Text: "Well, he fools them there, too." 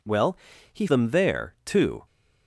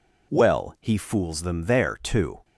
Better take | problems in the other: second | skips "fools"; at 0.8 s

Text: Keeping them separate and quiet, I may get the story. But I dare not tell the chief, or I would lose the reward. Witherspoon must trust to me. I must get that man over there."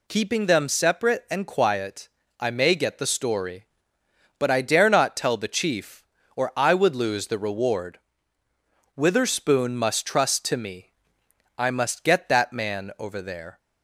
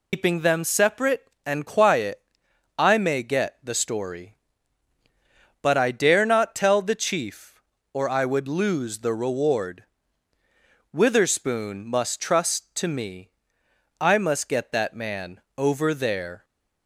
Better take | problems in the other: first | loses the start of "Keeping"; at 0.1 s; 145 ms // pauses between "man" and "over"; slight; at 15.3 s; 0.18 s long

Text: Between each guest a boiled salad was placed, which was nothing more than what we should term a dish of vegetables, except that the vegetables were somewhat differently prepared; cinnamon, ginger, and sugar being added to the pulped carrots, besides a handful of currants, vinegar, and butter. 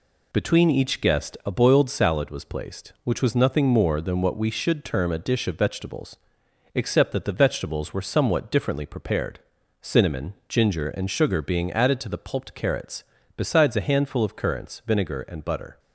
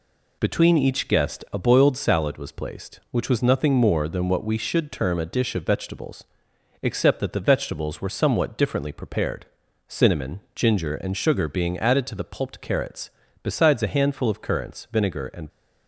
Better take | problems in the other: first | stops before "butter"; at 15.4 s

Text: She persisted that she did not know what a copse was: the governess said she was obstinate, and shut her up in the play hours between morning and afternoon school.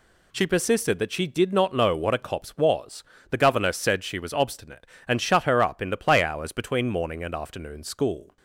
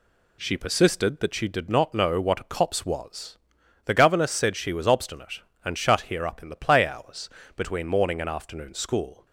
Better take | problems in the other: first | says "here" for "her"; at 6.0 s // pauses between "hours" and "between"; slight; at 7.2 s; 0.28 s long

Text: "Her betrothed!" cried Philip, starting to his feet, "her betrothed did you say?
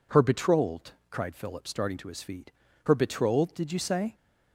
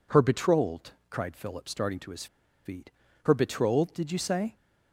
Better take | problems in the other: first | pauses between "his" and "feet"; at 2.2 s; 0.39 s long

